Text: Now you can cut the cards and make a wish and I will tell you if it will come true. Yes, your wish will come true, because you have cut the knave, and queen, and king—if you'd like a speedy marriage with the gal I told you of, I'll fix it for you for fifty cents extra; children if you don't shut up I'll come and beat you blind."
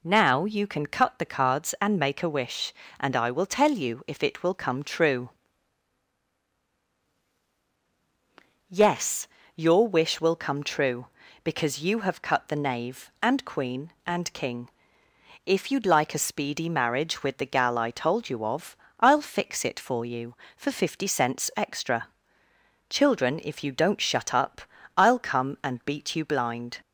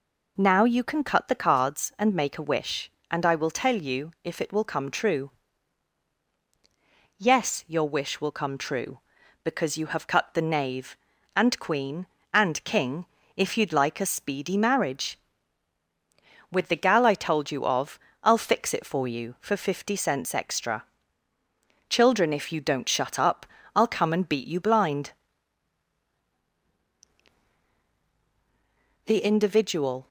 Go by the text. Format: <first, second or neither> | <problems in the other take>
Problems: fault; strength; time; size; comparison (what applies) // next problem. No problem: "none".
first | pauses between "up" and "I'll"; slight; at 23.4 s; 0.28 s long; slight in the first // goes on to say "The Individual"; noticeable; from 29.0 s on; 1.0 s long